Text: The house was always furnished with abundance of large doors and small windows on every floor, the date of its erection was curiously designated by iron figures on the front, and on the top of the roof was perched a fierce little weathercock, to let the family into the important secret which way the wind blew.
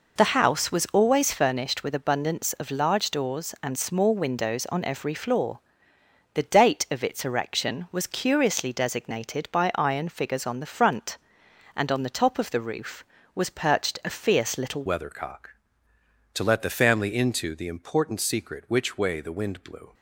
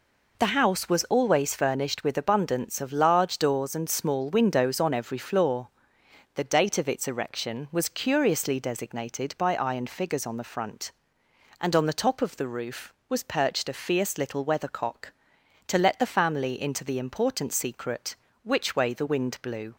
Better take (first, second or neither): second